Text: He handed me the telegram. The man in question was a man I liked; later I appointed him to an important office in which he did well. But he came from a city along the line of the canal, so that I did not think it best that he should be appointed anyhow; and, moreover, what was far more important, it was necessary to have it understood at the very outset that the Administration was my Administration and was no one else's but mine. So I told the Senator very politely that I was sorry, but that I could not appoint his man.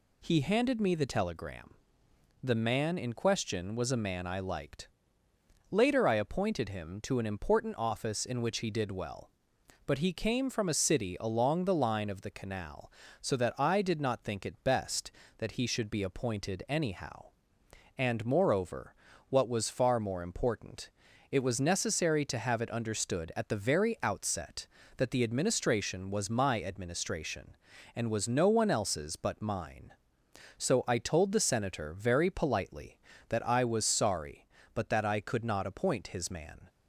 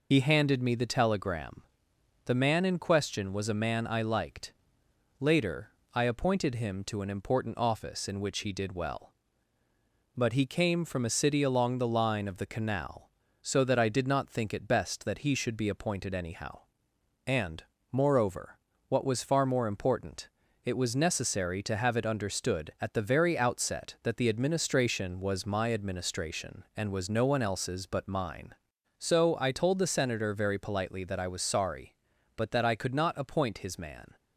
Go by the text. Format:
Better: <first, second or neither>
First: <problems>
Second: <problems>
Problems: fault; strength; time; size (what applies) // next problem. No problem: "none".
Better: first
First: none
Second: loses the start of "He"; at 0.1 s; 50 ms // pauses between "later" and "I"; slight; at 5.7 s; 0.24 s long